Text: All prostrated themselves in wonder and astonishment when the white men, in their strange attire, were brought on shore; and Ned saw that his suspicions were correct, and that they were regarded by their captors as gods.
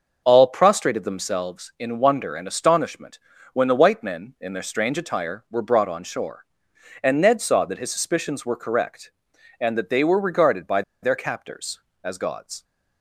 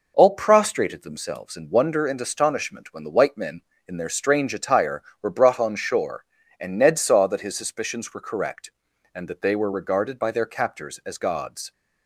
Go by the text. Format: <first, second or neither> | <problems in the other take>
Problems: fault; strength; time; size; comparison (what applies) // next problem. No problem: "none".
second | starts louder than the rest; until 1.2 s; 6 dB // pauses between "astonishment" and "when"; slight; at 3.1 s; 0.34 s long // pauses between "by" and "their"; slight; at 10.8 s; 0.21 s long